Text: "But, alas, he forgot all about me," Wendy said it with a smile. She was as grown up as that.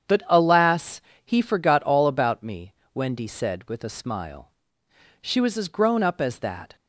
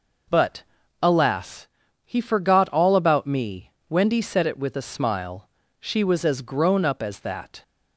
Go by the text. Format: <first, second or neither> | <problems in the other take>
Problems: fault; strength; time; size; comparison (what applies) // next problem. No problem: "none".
second | starts louder than the rest; strong; until 1.3 s; 8.5 dB // skips "it"; at 3.6 s